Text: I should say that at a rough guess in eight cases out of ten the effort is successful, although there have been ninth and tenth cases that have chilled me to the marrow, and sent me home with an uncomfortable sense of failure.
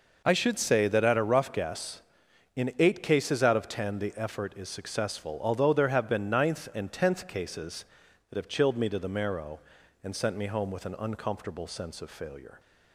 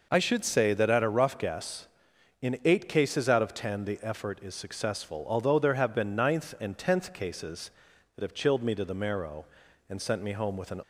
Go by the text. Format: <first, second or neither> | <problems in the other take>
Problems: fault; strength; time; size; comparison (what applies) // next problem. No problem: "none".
first | stops before "uncomfortable sense of failure"; at 10.8 s